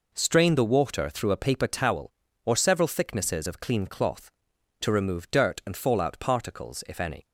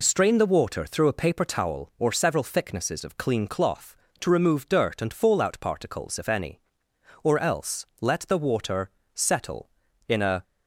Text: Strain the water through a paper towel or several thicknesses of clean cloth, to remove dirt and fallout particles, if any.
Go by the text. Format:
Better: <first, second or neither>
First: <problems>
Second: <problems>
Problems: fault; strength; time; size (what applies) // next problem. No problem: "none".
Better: first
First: none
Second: goes on to say "Or else let the water settle in a"; strong; from 7.2 s on; 3.2 s long